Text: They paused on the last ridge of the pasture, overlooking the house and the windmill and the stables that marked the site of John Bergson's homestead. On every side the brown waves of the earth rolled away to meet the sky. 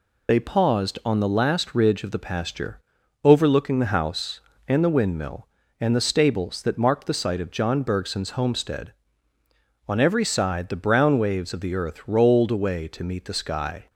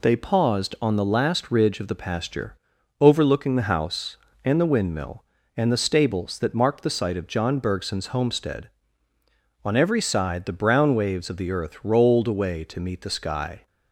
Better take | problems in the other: second | loses the start of "They"; at 0.2 s; 35 ms

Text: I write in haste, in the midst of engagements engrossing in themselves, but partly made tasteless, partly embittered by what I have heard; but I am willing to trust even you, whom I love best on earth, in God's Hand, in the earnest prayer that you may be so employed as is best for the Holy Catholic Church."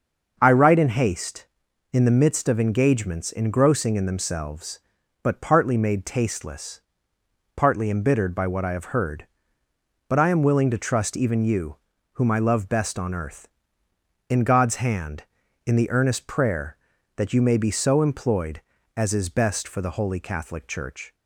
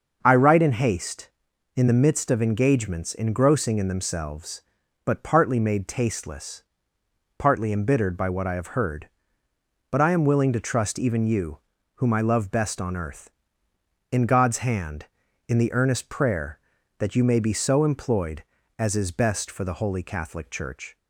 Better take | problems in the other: neither | starts louder than the rest; the same in both

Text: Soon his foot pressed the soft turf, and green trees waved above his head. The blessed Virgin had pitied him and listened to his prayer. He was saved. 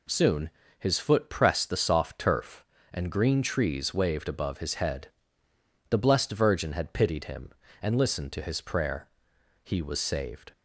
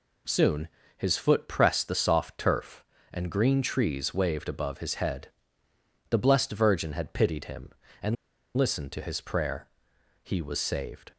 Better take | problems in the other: first | pauses between "Soon" and "his"; slight; at 0.6 s; 0.30 s long; slight in the first // pauses between "and" and "listened"; at 8.1 s; 0.42 s long

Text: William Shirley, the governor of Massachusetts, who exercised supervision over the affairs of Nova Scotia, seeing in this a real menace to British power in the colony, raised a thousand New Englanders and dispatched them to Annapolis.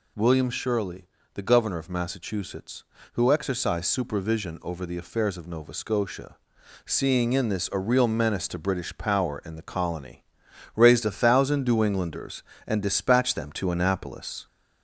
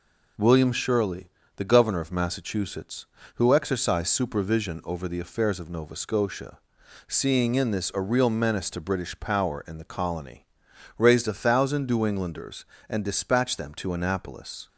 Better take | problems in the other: second | gets louder; slight; throughout; 2 dB

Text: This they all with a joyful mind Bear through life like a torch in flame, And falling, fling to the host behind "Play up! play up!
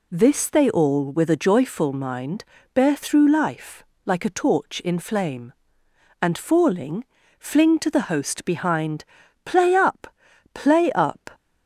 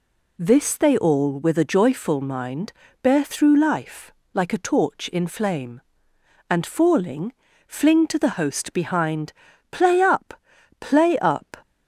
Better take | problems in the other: neither | pauses between "mind" and "Bear"; slight; the same in both // pauses between "life" and "like"; slight; the same in both // pauses between "behind" and "Play"; the same in both

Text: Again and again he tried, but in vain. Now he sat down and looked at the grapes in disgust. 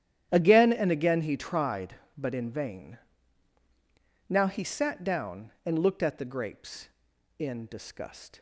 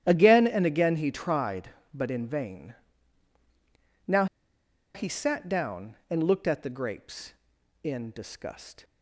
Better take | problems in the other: first | starts louder than the rest; strong; until 1.0 s; 11 dB; strong in the first // pauses between "Now" and "he"; noticeable; at 4.2 s; 0.69 s long

